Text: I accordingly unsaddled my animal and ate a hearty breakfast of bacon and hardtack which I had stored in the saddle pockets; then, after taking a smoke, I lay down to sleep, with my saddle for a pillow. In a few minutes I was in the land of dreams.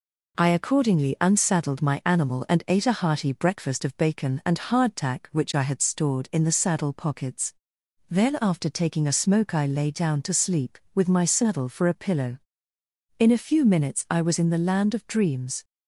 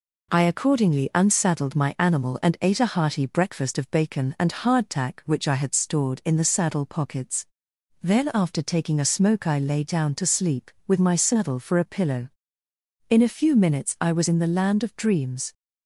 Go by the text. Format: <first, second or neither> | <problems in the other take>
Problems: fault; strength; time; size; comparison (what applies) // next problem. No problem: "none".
neither | none